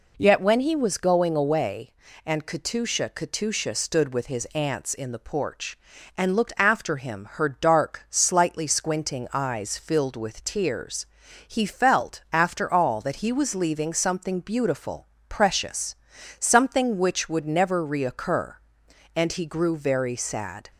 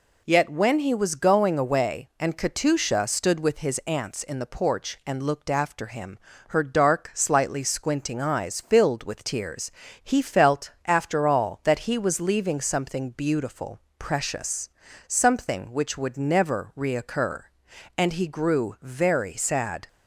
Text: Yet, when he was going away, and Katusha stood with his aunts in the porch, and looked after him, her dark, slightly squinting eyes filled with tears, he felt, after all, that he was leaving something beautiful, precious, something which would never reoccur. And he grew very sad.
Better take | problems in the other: second | says "Katusha" twice; at 3.1 s

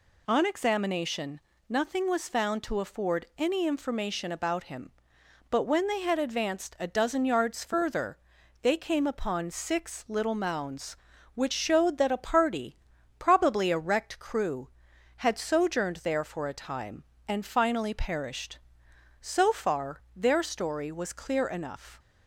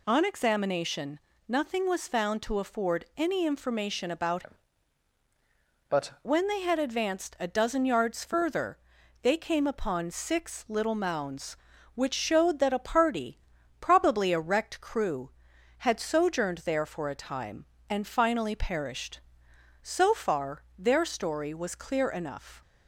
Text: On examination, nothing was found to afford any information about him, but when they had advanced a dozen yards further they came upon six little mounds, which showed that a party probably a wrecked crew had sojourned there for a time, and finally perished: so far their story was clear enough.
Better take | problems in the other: first | changes voice from "him" to "but"; from 4.4 to 6.0 s; 1.6 s long // pauses between "further" and "they"; at 8.7 s; 0.44 s long; also in the first // pauses between "party" and "probably"; at 13.3 s; 0.40 s long; also in the first

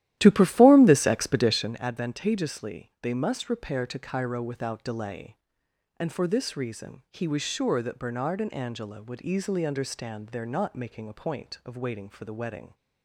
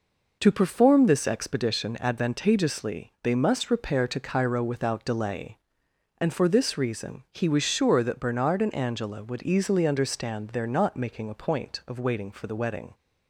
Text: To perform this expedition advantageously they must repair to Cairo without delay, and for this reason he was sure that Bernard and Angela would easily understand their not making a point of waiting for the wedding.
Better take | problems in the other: second | starts louder than the rest; strong; until 1.8 s; 13.5 dB

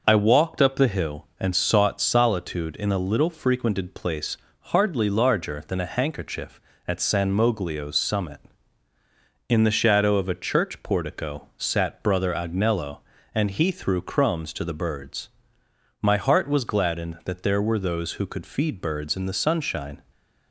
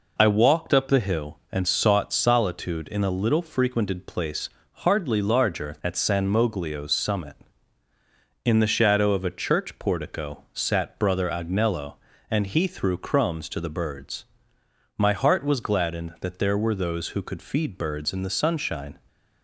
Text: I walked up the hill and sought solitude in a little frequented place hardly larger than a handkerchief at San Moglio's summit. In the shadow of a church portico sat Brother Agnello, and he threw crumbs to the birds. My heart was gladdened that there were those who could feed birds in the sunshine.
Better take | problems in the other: first | pauses between "place" and "hardly"; slight; at 4.4 s; 0.24 s long; slight in the first // skips "than a handkerchief"; at 5.7 s

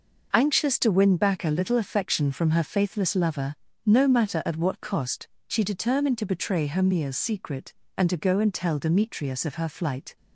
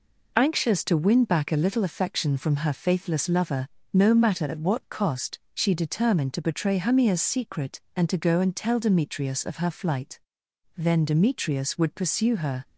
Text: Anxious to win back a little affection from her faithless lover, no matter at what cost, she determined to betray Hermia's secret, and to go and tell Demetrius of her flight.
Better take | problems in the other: first | goes on to say "Then Demetrius would pursue her"; strong; from 10.7 s on; 1.8 s long

